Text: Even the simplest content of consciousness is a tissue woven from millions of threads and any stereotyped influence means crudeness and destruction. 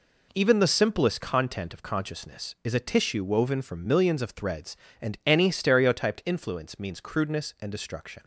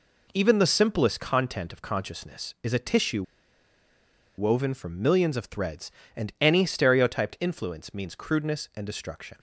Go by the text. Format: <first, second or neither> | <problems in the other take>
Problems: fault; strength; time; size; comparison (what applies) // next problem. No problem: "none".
first | pauses between "tissue" and "woven"; at 3.2 s; 1.1 s long